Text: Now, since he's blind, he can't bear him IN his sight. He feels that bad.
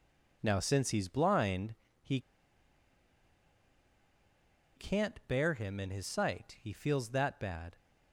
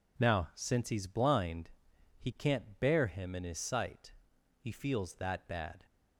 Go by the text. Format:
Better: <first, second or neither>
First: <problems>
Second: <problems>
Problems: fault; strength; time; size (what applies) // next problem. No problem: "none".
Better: second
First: pauses between "he" and "can't"; strong; at 2.1 s; 2.5 s long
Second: none